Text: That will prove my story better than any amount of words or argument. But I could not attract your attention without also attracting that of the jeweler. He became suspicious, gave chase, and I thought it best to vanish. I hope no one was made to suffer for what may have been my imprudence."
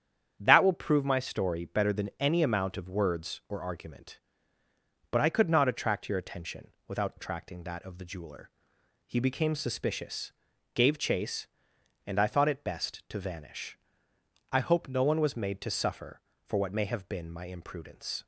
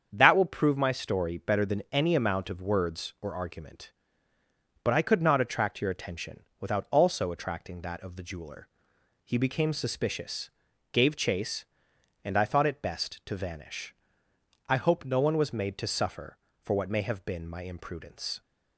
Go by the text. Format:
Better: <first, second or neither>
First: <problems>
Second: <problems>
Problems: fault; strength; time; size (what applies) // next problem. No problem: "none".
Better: second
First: starts louder than the rest; strong; until 1.3 s; 8.5 dB // pauses between "attention" and "without"; slight; at 6.6 s; 0.18 s long // skips "also"; at 7.1 s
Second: starts louder than the rest; strong; until 1.1 s; 7.5 dB // pauses between "attention" and "without"; slight; at 6.4 s; 0.18 s long